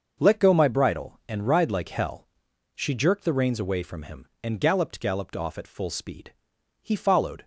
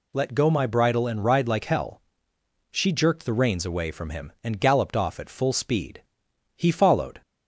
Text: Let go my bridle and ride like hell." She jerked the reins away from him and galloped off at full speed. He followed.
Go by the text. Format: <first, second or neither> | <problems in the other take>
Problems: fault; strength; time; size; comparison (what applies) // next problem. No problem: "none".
second | starts louder than the rest; until 1.2 s; 6.5 dB // says "galloped" twice; at 4.9 s